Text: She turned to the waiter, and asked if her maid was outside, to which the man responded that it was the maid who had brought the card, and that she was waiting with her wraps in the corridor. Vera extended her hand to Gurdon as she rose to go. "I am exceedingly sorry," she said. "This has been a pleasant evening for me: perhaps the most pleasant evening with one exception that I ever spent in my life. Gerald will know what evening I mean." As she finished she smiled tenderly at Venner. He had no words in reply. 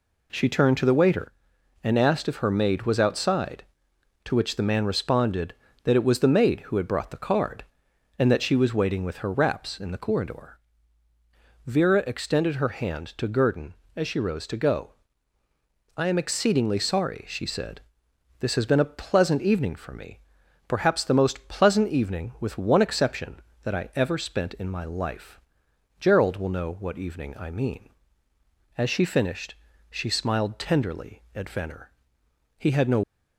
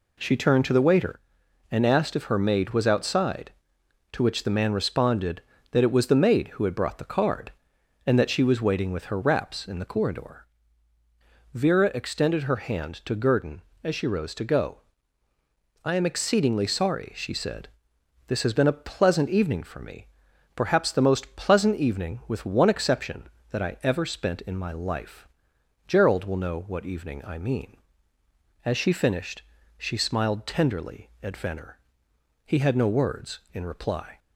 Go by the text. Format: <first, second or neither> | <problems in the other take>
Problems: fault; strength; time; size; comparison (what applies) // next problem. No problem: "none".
second | pauses between "finished" and "she"; at 29.5 s; 0.38 s long; also in the second // stops before "words in reply"; at 33.0 s